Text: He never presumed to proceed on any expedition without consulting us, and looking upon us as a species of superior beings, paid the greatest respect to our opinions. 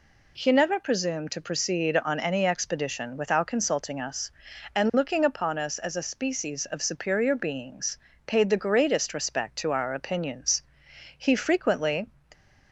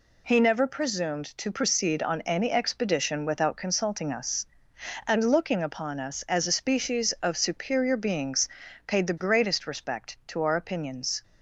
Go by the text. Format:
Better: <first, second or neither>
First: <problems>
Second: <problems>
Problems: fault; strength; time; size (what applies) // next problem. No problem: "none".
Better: second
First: goes on to say "He frequently"; noticeable; from 11.1 s on; 0.90 s long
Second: none